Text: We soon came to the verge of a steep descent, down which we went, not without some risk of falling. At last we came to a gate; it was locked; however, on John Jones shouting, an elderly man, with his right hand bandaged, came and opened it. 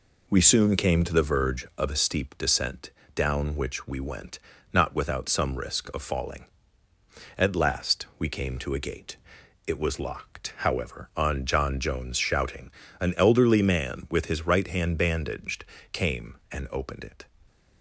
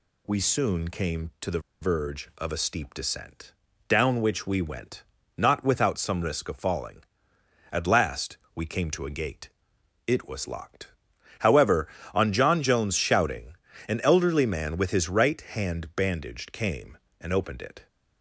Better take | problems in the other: first | pauses between "the" and "verge"; slight; at 1.5 s; 0.22 s long // pauses between "last" and "we"; slight; at 8.3 s; 0.18 s long

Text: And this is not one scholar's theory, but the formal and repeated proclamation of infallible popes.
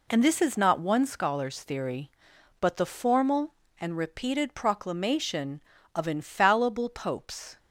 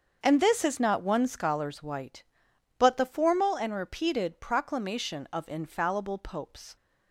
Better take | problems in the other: first | starts louder than the rest; until 1.2 s; 6.5 dB // says "white" for "theory"; at 1.8 s

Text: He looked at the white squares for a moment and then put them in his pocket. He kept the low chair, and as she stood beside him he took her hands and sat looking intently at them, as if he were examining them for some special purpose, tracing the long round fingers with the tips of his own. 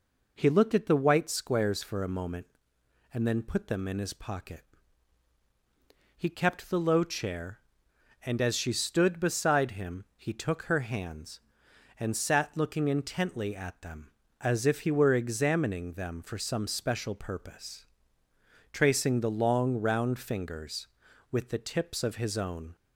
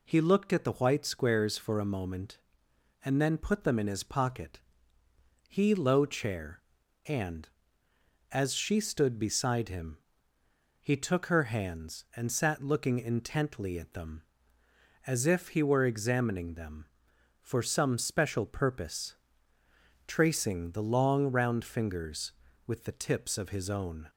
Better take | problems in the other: first | skips "kept the"; at 5.7 s // pauses between "him" and "he"; noticeable; at 9.9 s; 0.82 s long

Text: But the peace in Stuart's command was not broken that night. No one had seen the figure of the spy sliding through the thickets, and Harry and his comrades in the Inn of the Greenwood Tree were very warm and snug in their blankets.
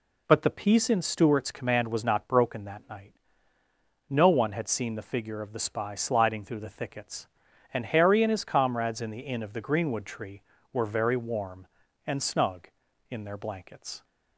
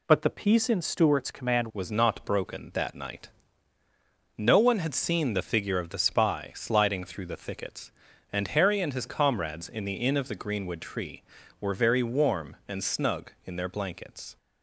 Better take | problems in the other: first | changes voice at "was"; from 1.7 s on; 12.6 s long

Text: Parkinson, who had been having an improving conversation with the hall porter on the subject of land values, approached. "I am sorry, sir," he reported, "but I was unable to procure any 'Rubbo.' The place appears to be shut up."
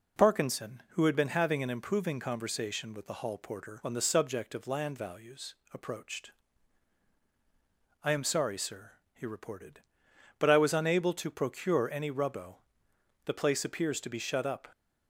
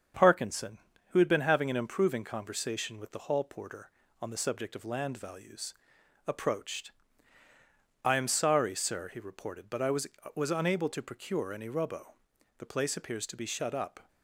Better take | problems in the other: first | starts louder than the rest; until 1.4 s; 7 dB // says "was" twice; at 10.3 s

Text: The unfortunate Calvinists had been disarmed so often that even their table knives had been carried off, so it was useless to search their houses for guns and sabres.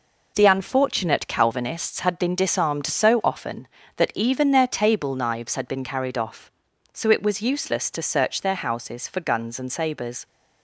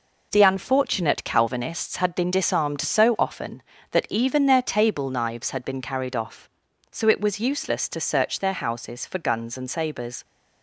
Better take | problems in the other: neither | none

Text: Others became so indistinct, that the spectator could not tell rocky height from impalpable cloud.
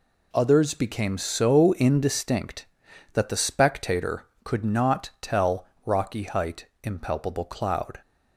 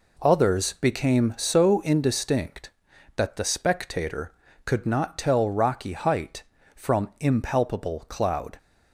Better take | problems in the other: second | pauses between "tell" and "rocky"; slight; at 5.6 s; 0.18 s long // skips "from"; at 6.7 s

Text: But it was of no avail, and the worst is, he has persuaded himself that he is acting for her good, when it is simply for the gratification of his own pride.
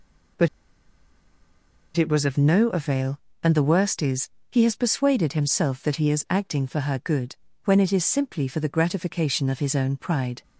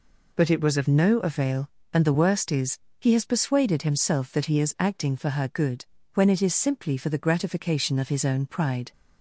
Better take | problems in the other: second | pauses between "But" and "it"; strong; at 0.4 s; 1.4 s long

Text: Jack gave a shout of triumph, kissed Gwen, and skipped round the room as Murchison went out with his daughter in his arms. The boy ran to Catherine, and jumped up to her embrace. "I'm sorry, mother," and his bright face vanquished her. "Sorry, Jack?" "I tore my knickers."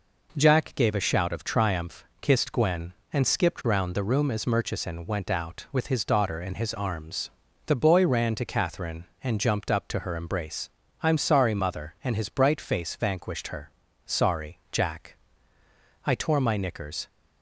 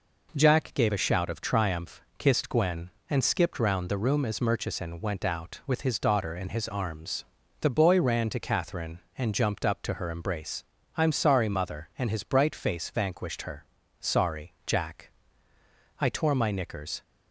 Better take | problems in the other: neither | none

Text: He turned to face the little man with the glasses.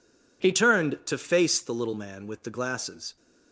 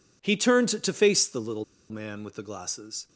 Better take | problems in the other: first | pauses between "little" and "man"; slight; at 1.6 s; 0.25 s long

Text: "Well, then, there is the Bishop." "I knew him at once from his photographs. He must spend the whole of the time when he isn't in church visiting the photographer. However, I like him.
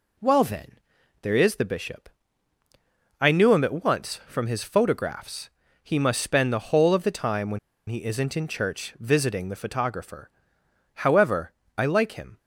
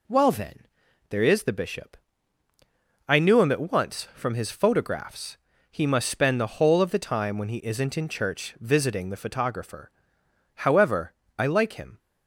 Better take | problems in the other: second | pauses between "when" and "he"; slight; at 7.5 s; 0.30 s long

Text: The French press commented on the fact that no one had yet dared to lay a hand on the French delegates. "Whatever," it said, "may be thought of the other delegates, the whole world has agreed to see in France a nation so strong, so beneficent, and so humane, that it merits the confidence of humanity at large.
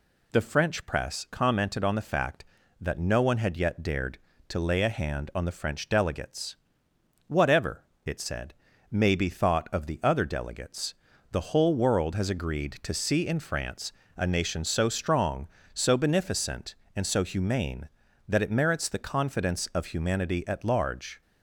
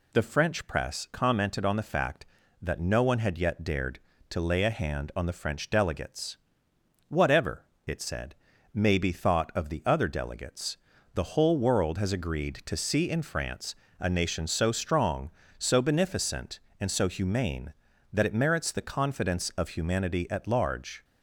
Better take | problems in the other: neither | pauses between "France" and "a"; slight; the same in both

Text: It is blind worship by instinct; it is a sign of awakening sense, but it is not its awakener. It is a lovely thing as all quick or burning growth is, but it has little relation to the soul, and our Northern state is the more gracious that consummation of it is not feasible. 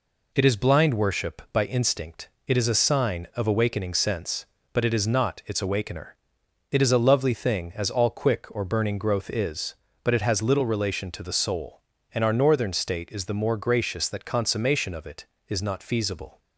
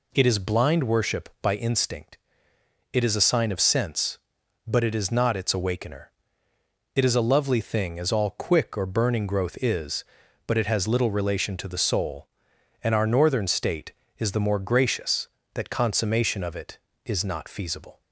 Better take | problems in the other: first | skips "awakening"; at 3.6 s

